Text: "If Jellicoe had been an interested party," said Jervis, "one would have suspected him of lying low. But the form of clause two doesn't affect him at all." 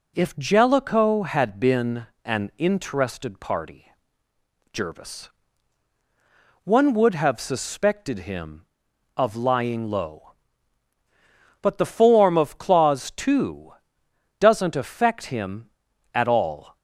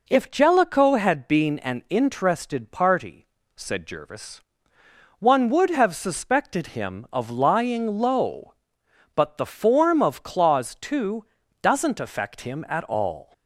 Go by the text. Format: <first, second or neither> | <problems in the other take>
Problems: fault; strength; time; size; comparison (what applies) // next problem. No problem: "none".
second | pauses between "been" and "an"; slight; at 2.0 s; 0.18 s long // skips "said"; at 4.3 s // pauses between "two" and "doesn't"; noticeable; at 13.7 s; 0.66 s long; slight in the second